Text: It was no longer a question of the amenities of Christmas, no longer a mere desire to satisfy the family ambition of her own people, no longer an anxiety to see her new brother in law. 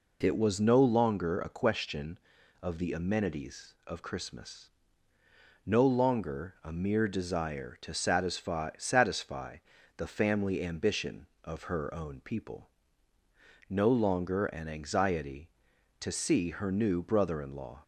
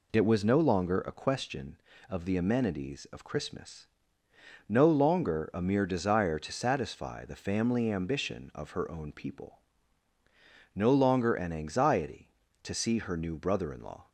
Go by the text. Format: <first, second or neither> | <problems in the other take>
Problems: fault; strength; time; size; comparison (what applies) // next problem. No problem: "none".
second | says "satisfy" twice; at 8.7 s